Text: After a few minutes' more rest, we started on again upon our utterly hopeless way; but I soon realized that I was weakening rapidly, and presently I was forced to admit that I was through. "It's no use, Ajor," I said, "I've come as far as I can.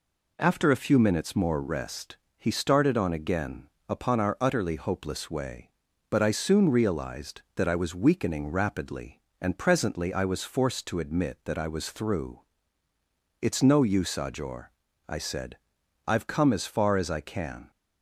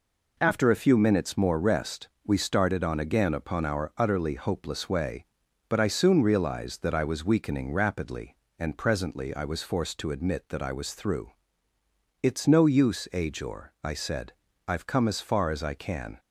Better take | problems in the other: second | says "he" for "we"; at 2.3 s // pauses between "again" and "upon"; slight; at 3.6 s; 0.20 s long

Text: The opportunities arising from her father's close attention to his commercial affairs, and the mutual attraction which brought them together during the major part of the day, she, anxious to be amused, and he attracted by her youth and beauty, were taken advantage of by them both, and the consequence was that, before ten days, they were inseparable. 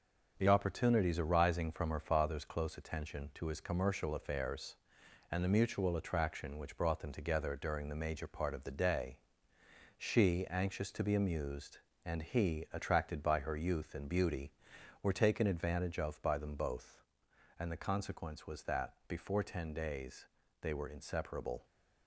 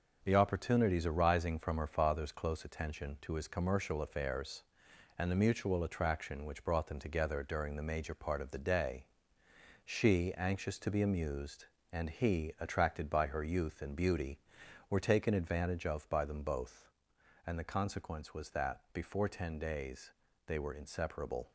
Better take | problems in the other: neither | none

